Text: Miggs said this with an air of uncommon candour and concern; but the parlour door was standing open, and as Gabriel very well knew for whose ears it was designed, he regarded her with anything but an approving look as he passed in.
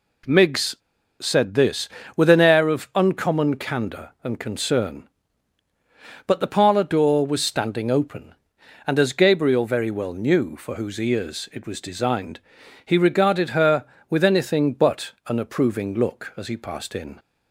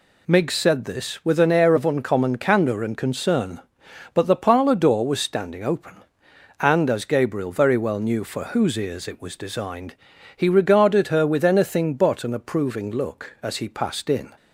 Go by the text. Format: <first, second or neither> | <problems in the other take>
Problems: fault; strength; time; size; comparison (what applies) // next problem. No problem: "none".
second | pauses between "Miggs" and "said"; at 0.7 s; 0.45 s long // pauses between "but" and "an"; slight; at 15.1 s; 0.16 s long